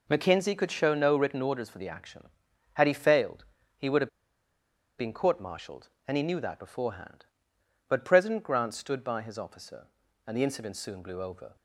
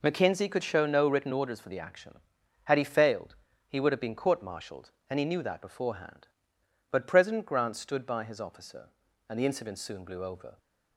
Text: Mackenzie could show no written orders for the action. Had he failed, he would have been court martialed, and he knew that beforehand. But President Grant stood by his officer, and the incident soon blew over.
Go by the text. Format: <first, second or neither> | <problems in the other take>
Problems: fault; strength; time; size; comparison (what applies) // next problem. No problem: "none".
second | pauses between "have" and "been"; noticeable; at 4.0 s; 0.89 s long